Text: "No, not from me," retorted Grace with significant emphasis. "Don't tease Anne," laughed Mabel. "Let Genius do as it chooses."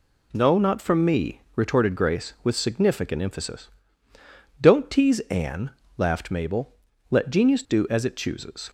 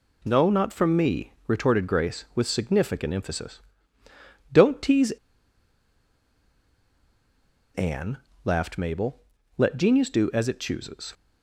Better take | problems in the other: first | pauses between "tease" and "Anne"; strong; at 5.0 s; 2.6 s long

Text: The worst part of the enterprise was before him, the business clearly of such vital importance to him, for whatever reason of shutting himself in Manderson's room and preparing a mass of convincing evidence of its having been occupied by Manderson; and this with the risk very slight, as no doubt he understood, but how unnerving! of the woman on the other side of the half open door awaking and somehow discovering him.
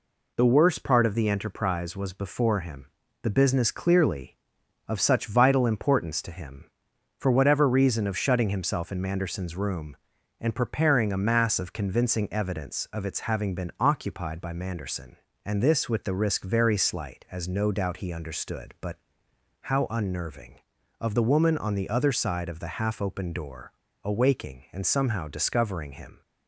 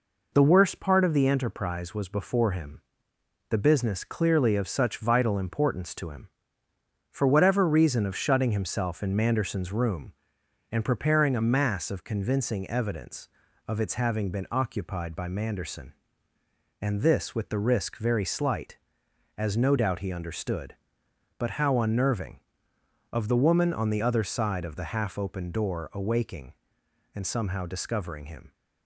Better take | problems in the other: second | pauses between "but" and "how"; noticeable; at 18.9 s; 0.64 s long // pauses between "door" and "awaking"; slight; at 23.7 s; 0.33 s long

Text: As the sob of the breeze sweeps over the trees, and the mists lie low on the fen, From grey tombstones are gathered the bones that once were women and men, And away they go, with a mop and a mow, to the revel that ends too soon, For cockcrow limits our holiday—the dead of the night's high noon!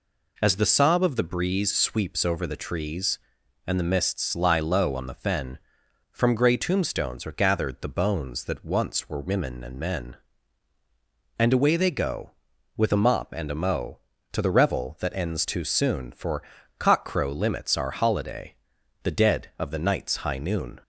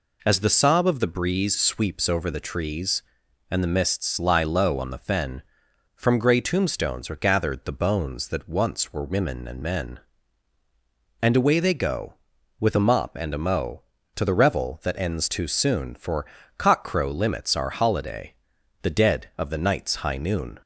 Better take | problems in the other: neither | pauses between "For" and "cockcrow"; slight; the same in both

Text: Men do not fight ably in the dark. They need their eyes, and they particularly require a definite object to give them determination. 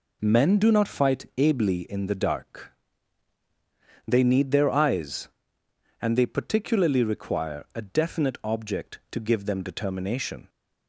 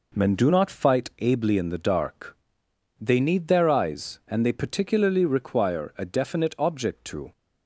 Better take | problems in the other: first | stops before "give them determination"; at 7.3 s

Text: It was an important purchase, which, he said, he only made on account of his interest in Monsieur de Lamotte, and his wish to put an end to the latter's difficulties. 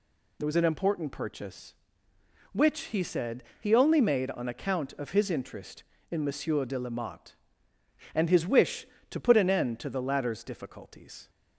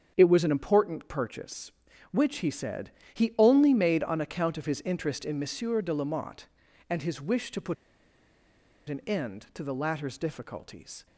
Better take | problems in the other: first | starts louder than the rest; strong; until 1.1 s; 7.5 dB // pauses between "put" and "an"; at 7.7 s; 1.1 s long

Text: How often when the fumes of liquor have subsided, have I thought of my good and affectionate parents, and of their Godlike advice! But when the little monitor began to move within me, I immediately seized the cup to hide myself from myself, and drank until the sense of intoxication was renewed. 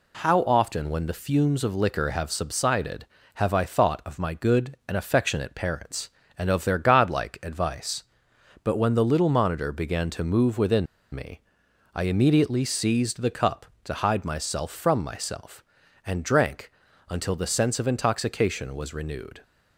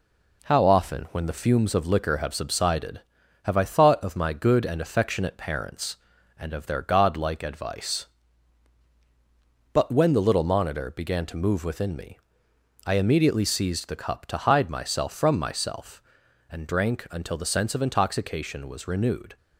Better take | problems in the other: second | pauses between "within" and "me"; slight; at 10.8 s; 0.27 s long // pauses between "drank" and "until"; slight; at 16.7 s; 0.36 s long

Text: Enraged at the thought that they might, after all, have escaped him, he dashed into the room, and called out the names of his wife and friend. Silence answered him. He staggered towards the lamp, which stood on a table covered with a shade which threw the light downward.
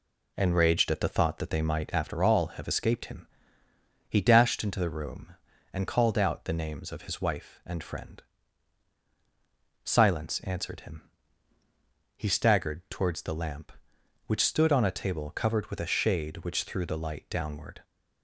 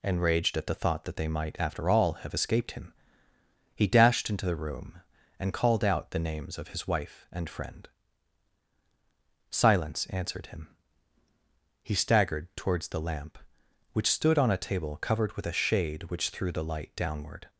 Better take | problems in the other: second | starts louder than the rest; slight; until 2.2 s; 2.5 dB

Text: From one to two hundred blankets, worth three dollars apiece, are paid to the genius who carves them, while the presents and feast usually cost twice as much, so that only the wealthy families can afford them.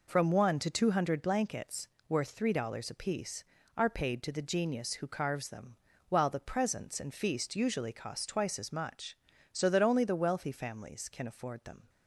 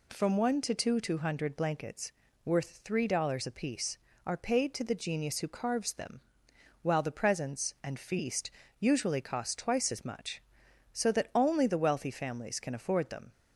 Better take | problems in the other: first | says "two" twice; at 1.0 s // pauses between "feast" and "usually"; slight; at 8.4 s; 0.30 s long

